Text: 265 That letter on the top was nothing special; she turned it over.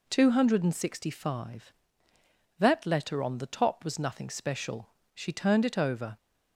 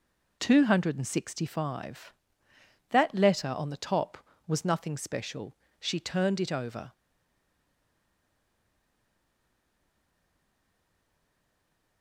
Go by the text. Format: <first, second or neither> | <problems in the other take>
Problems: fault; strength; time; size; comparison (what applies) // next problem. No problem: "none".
first | stays silent after the last word; strong; from 6.9 s on; 5.1 s long